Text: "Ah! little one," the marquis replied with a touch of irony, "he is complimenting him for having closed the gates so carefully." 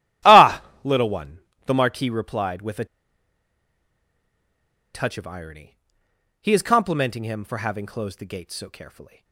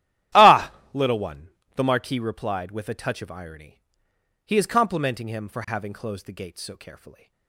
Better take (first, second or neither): second